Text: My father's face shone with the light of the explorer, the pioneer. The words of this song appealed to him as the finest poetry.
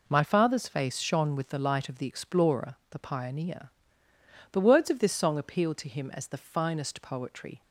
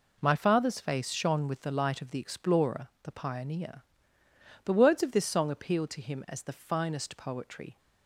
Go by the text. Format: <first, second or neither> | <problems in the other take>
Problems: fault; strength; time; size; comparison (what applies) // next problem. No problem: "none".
neither | none